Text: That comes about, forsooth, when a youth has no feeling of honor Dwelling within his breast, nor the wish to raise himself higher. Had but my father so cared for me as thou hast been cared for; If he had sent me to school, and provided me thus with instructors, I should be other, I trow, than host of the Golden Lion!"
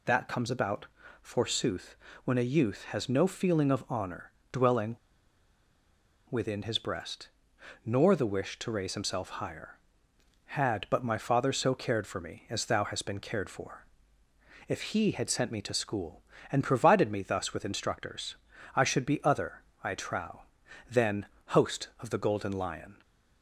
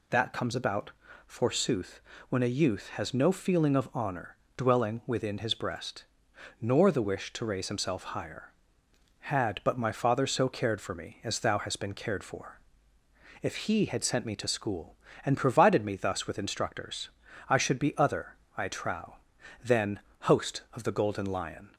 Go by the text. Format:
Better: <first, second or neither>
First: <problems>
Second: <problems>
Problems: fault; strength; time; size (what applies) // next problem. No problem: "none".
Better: second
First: pauses between "honor" and "Dwelling"; slight; at 4.2 s; 0.22 s long // pauses between "Dwelling" and "within"; strong; at 4.9 s; 1.3 s long // pauses between "than" and "host"; slight; at 21.2 s; 0.22 s long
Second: pauses between "honor" and "Dwelling"; slight; at 4.3 s; 0.22 s long // pauses between "than" and "host"; slight; at 19.9 s; 0.22 s long